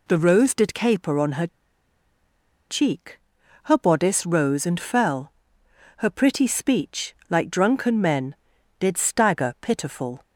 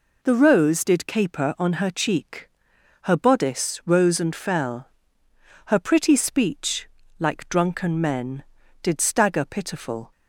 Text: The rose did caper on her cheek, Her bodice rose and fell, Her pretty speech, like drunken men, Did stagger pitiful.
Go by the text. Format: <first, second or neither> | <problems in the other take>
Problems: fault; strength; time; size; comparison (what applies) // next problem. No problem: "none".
second | pauses between "her" and "cheek"; at 1.4 s; 1.2 s long